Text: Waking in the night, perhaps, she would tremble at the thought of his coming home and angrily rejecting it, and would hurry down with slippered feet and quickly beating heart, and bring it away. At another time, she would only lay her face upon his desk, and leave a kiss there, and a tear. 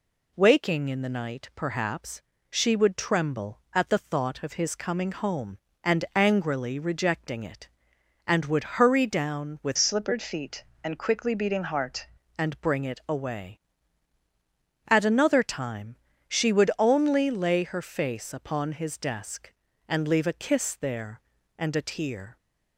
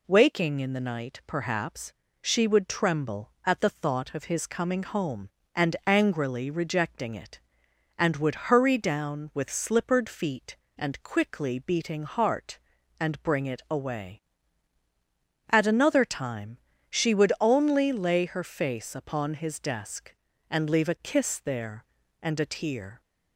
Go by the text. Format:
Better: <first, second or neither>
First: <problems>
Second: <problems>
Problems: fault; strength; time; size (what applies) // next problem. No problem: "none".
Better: second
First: changes voice from "slippered" to "heart"; from 9.7 to 12.0 s; 2.3 s long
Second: none